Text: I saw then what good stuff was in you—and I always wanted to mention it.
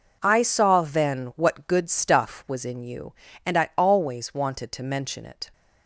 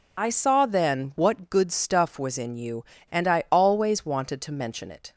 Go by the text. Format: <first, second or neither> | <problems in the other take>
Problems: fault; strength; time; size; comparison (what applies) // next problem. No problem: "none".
first | loses the start of "I"; at 0.1 s; 40 ms